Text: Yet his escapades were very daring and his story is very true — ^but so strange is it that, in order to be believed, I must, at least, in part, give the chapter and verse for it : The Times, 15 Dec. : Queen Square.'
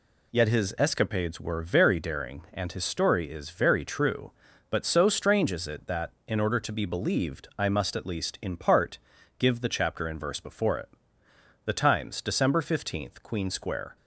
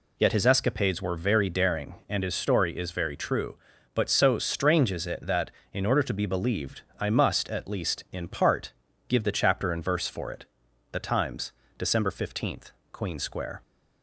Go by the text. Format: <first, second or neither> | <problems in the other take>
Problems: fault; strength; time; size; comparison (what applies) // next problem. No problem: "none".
second | says "before" for "for"; at 10.3 s